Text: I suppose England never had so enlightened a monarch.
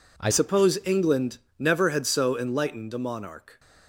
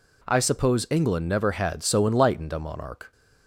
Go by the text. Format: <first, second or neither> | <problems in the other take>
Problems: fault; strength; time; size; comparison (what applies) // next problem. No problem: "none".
second | changes voice at "suppose"; from 0.3 s on; 3.2 s long // pauses between "England" and "never"; slight; at 1.3 s; 0.22 s long